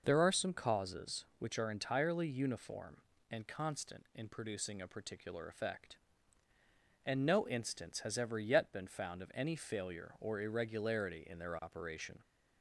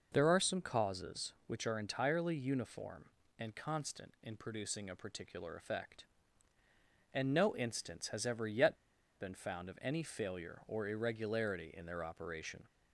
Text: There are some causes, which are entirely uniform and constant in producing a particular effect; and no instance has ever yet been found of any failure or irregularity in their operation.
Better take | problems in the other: first | pauses between "yet" and "been"; at 8.7 s; 0.41 s long

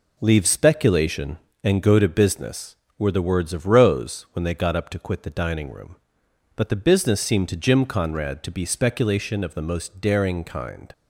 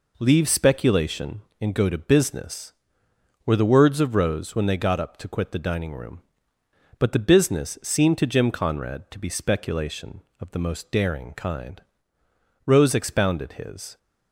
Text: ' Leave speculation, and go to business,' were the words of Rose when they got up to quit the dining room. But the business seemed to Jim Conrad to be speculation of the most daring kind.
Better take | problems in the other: first | goes on to say "Rose expounded his"; from 12.6 s on; 1.3 s long

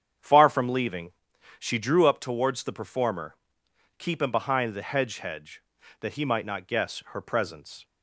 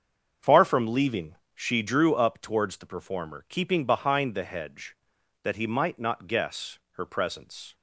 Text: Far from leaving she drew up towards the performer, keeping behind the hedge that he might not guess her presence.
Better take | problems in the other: second | starts louder than the rest; strong; until 1.7 s; 8 dB; also in the second // pauses between "leaving" and "she"; noticeable; at 1.1 s; 0.50 s long; slight in the second // says "hedge" twice; at 5.1 s

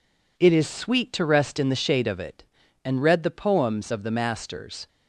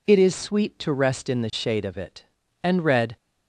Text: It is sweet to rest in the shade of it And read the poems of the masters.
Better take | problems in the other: first | stops before "the poems of the masters"; at 3.1 s

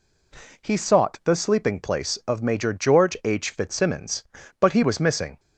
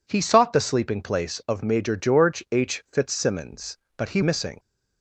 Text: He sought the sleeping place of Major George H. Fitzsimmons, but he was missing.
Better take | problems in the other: first | skips "was"; at 4.2 s

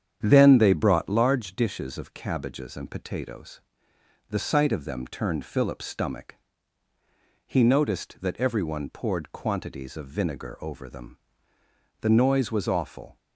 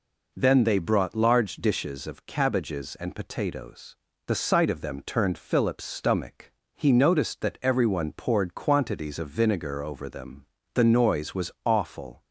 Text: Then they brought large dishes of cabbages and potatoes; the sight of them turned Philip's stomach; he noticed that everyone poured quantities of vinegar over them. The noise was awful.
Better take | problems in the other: second | starts louder than the rest; strong; until 1.2 s; 8.5 dB

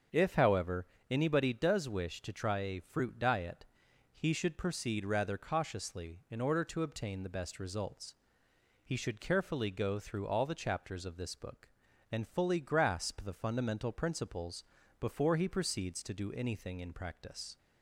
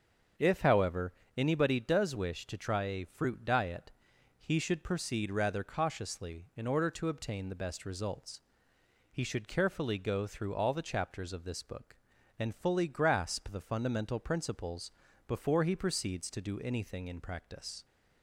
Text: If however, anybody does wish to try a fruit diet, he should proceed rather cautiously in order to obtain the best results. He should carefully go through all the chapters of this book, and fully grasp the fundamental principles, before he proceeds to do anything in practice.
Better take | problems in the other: neither | starts louder than the rest; the same in both

